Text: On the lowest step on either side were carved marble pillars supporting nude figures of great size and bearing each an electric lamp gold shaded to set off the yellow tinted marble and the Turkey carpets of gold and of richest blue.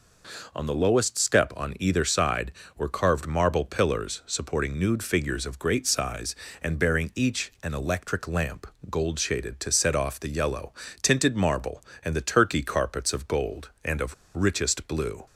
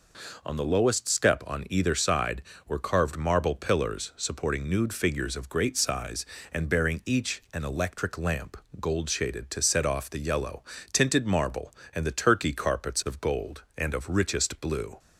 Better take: second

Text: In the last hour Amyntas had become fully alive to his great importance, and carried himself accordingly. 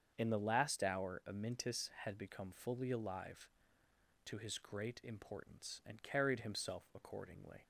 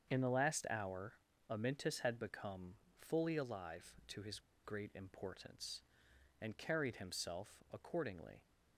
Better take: first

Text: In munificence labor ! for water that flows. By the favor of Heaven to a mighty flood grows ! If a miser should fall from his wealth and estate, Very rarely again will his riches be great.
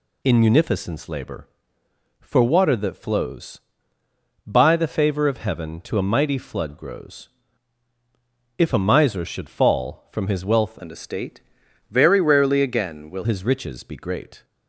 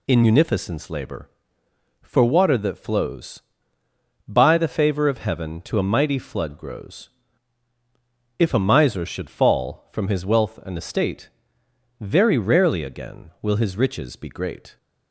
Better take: second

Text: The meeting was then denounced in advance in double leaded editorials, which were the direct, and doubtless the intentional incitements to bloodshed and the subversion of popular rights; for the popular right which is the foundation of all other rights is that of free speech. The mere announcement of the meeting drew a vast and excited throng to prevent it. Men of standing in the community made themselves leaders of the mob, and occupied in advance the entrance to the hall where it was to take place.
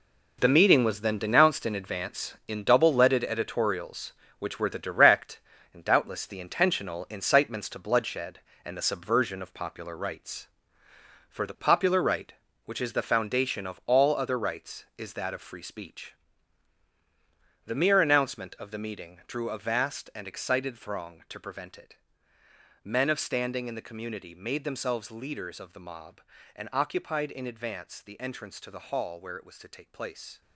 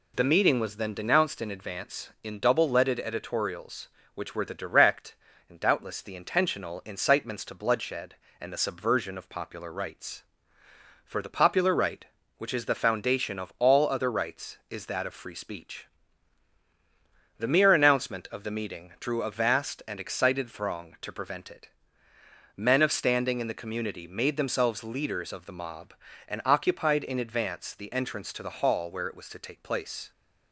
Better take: second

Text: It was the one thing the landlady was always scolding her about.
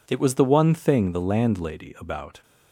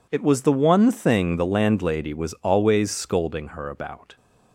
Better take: second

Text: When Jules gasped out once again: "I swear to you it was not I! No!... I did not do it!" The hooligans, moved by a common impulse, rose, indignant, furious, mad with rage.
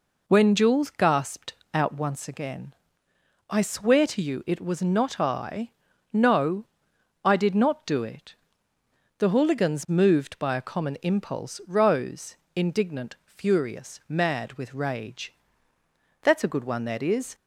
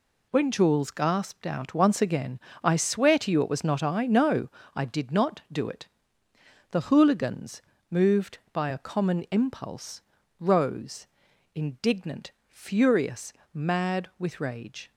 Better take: second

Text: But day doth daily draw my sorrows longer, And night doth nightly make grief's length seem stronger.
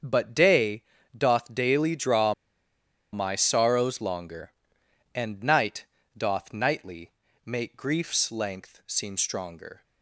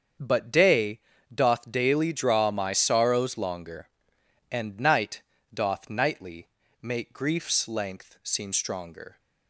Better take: second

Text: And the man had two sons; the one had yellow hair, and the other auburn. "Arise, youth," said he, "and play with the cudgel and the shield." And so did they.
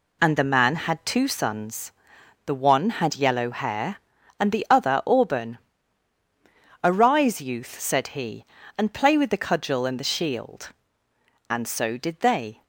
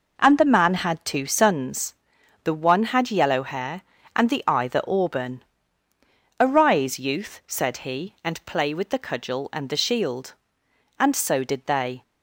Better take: first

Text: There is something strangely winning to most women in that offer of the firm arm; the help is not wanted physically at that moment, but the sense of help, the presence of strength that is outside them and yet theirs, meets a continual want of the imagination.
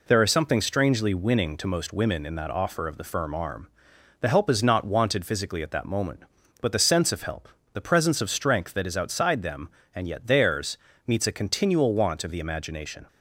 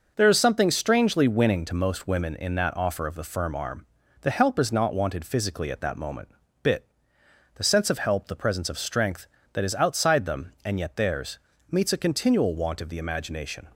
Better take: first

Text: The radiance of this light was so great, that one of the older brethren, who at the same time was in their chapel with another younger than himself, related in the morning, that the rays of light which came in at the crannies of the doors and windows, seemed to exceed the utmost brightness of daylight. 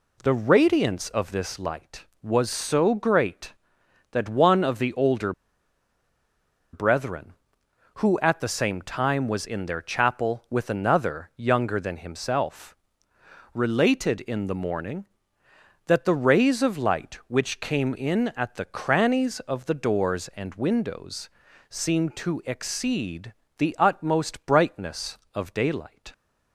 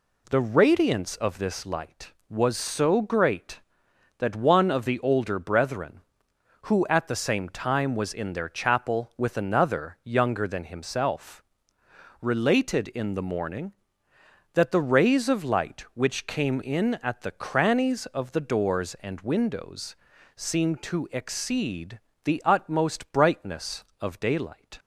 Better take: second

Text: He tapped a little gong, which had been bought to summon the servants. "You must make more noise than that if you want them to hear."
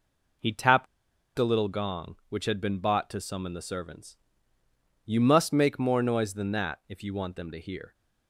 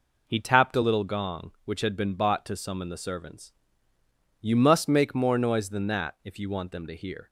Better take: second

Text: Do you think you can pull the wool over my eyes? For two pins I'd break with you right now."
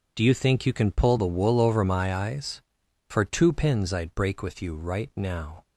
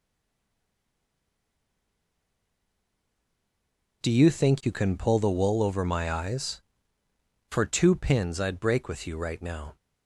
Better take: first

